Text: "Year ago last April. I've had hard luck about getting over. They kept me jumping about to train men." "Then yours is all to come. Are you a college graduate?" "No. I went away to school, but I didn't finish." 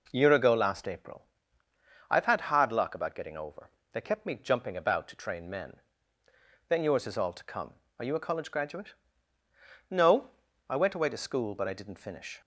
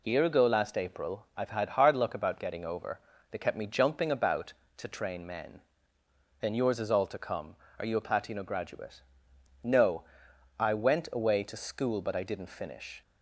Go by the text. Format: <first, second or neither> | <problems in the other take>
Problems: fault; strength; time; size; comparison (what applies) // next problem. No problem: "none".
first | says "platino" for "college"; at 8.0 s